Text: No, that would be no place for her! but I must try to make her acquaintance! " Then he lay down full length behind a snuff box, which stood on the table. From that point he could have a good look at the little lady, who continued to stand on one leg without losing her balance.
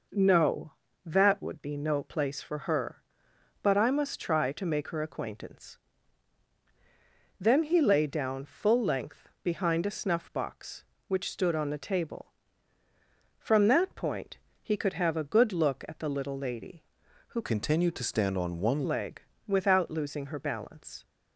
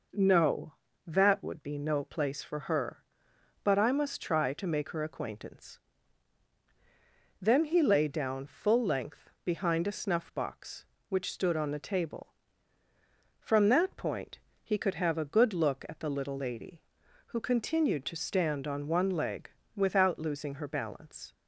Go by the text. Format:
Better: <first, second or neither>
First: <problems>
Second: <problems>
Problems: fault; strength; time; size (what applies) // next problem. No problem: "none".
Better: second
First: pauses between "point" and "he"; slight; at 14.3 s; 0.24 s long // changes voice from "continued" to "one"; from 17.4 to 18.8 s; 1.4 s long // pauses between "leg" and "without"; slight; at 19.2 s; 0.26 s long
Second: pauses between "point" and "he"; slight; at 14.4 s; 0.24 s long // pauses between "leg" and "without"; slight; at 19.4 s; 0.26 s long